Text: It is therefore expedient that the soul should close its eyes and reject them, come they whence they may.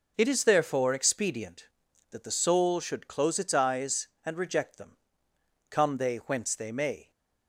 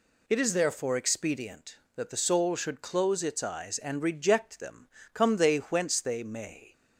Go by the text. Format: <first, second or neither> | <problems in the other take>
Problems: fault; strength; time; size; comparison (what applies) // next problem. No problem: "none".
neither | none